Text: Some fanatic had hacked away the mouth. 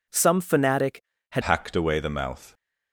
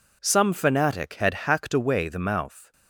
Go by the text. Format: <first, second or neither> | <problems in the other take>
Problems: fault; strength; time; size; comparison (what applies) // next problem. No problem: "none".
second | changes voice at "hacked"; from 1.4 s on; 1.1 s long